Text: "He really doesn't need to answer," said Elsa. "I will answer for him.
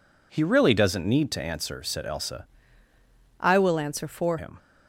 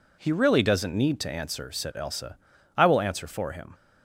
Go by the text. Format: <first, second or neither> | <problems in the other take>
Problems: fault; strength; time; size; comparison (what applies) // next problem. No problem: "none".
second | changes voice from "I" to "for"; from 3.4 to 4.3 s; 0.9 s long